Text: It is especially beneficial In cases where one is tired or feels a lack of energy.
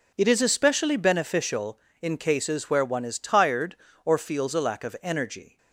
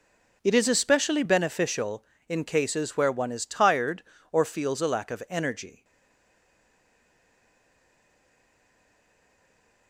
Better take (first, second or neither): first